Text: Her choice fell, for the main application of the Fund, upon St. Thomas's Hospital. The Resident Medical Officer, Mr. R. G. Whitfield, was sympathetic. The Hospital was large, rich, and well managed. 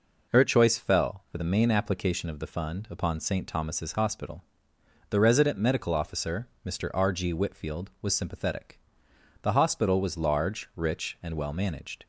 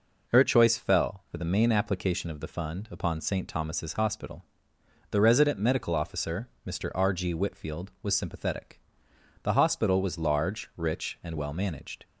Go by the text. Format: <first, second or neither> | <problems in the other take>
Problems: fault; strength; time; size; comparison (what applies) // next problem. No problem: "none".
neither | none